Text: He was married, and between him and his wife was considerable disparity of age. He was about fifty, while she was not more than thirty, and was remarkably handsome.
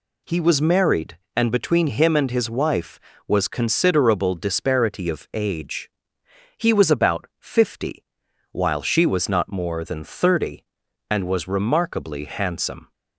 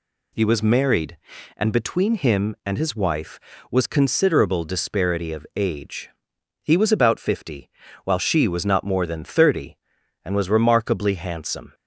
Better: neither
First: none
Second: none

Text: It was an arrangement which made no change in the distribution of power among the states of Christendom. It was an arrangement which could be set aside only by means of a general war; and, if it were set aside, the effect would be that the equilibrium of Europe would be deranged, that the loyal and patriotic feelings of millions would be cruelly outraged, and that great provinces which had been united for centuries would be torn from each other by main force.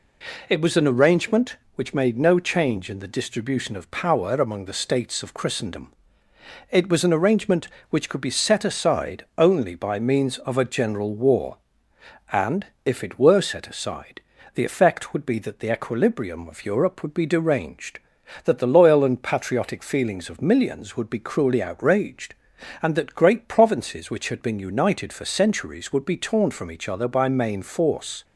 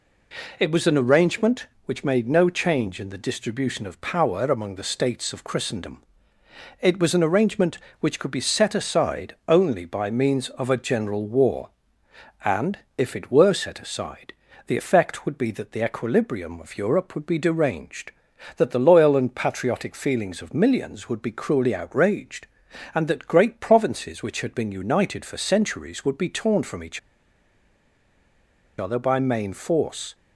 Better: first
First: none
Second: pauses between "each" and "other"; strong; at 26.9 s; 1.8 s long

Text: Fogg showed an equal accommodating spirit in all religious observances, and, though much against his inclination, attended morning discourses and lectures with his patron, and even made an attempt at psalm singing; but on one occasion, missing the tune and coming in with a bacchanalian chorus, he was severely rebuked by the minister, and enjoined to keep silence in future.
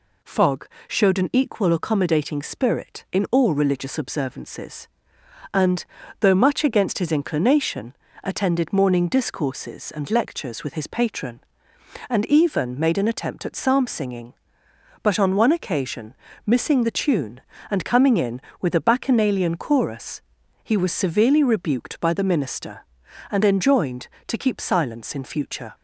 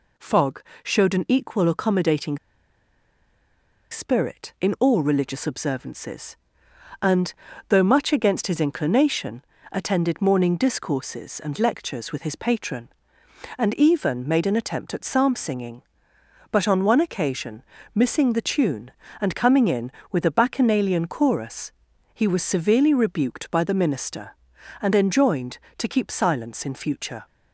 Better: first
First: pauses between "Fogg" and "showed"; slight; at 0.6 s; 0.22 s long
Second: pauses between "Fogg" and "showed"; slight; at 0.6 s; 0.22 s long // pauses between "accommodating" and "spirit"; strong; at 2.3 s; 1.5 s long

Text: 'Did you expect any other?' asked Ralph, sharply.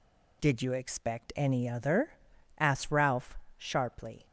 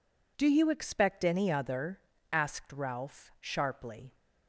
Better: first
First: none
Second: says "Do" for "Did"; at 0.3 s

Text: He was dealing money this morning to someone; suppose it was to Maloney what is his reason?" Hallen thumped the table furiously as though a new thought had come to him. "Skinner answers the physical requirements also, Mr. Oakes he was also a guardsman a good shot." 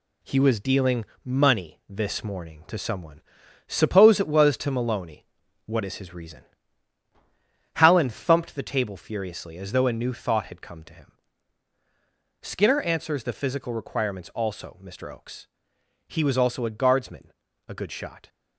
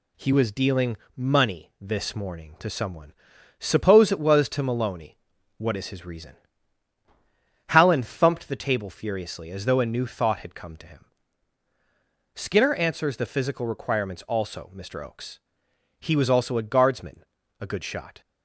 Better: second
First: gets quieter; noticeable; throughout; 4.5 dB // pauses between "dealing" and "money"; slight; at 1.0 s; 0.20 s long // pauses between "Maloney" and "what"; at 5.2 s; 0.40 s long // pauses between "Oakes" and "he"; noticeable; at 15.4 s; 0.60 s long // pauses between "guardsman" and "a"; slight; at 17.3 s; 0.34 s long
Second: pauses between "dealing" and "money"; slight; at 0.9 s; 0.20 s long // pauses between "Maloney" and "what"; at 5.1 s; 0.40 s long // pauses between "Oakes" and "he"; noticeable; at 15.3 s; 0.60 s long // pauses between "guardsman" and "a"; slight; at 17.2 s; 0.34 s long

